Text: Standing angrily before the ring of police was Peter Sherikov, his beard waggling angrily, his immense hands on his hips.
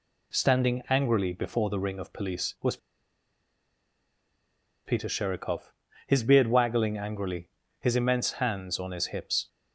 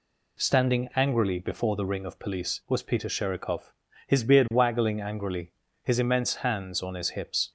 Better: second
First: pauses between "was" and "Peter"; strong; at 2.7 s; 2.0 s long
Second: none

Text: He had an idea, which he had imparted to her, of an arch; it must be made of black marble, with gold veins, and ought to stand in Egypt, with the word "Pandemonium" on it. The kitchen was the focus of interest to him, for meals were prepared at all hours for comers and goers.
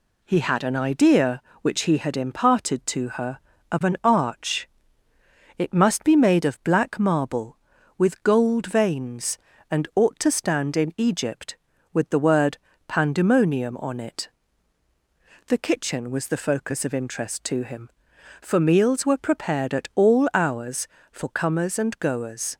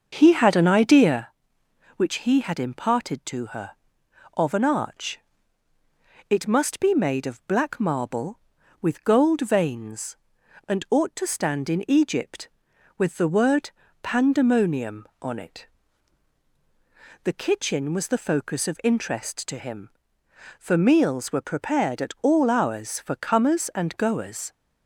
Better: first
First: pauses between "word" and "Pandemonium"; slight; at 12.5 s; 0.30 s long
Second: starts louder than the rest; until 1.3 s; 6.5 dB // pauses between "word" and "Pandemonium"; slight; at 13.7 s; 0.32 s long

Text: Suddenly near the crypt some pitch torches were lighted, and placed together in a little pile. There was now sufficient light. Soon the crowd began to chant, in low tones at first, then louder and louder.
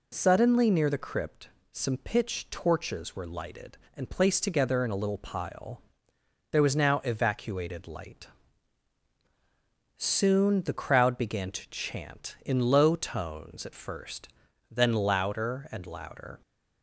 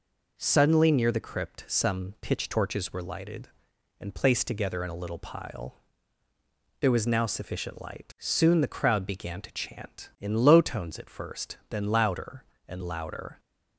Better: second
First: pauses between "crypt" and "some"; slight; at 1.4 s; 0.22 s long // says "evacuated" for "sufficient"; at 7.0 s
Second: none

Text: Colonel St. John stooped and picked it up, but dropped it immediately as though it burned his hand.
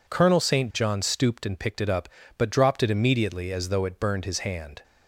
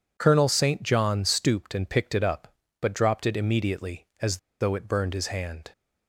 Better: first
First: none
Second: pauses between "as" and "though"; slight; at 4.3 s; 0.23 s long

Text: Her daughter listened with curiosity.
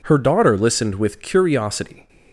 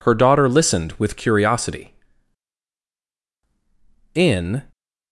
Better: first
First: none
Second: goes on to say "In"; slight; from 4.1 s on; 0.48 s long

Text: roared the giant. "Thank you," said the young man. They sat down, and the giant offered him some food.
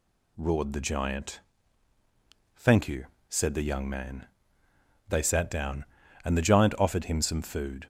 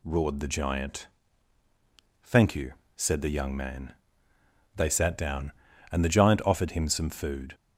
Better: neither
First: none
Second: none

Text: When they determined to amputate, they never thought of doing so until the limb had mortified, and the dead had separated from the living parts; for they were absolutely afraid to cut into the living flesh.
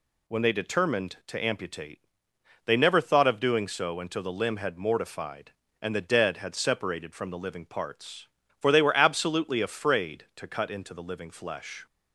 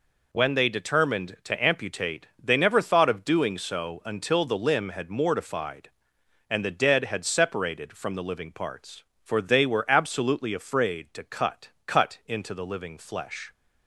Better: first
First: none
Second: says "cut" twice; at 11.8 s

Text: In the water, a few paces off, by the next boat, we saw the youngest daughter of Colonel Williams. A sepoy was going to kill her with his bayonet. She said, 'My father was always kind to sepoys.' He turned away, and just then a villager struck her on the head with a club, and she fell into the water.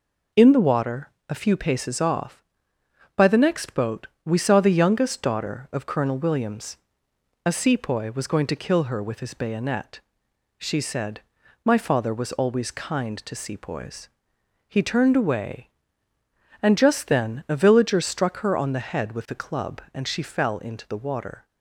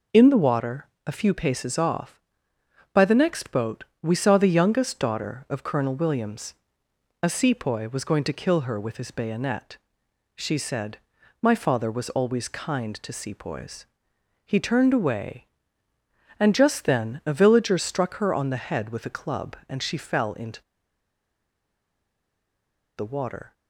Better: first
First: none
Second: pauses between "into" and "the"; strong; at 20.5 s; 2.3 s long

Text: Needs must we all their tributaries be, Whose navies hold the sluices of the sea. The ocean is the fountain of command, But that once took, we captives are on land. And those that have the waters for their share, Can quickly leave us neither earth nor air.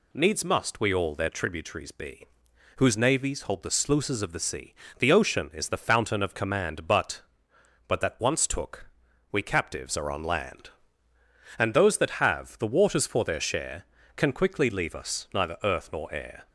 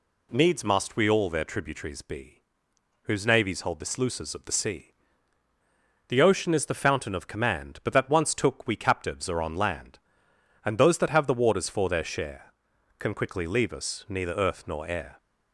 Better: second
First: says "But" twice; at 7.8 s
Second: none

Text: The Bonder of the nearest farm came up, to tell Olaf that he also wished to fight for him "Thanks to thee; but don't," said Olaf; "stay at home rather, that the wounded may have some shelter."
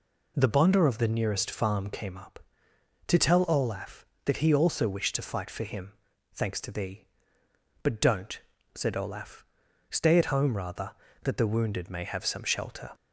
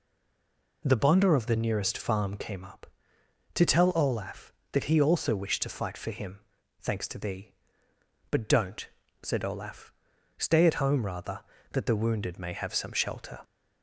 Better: first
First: pauses between "him" and "Thanks"; at 5.9 s; 0.40 s long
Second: stays silent before the first word; slight; until 0.8 s; 0.8 s long // pauses between "him" and "Thanks"; at 6.4 s; 0.40 s long

